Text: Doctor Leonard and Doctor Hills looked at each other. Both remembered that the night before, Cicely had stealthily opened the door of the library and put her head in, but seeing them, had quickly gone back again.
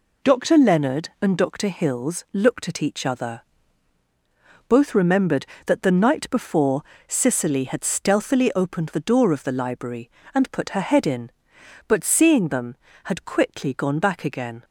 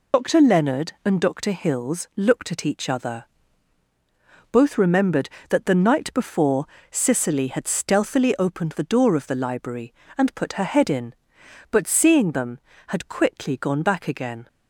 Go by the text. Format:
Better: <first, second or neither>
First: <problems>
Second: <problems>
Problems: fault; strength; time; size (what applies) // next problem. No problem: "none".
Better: first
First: none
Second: loses the start of "Doctor"; at 0.1 s; 70 ms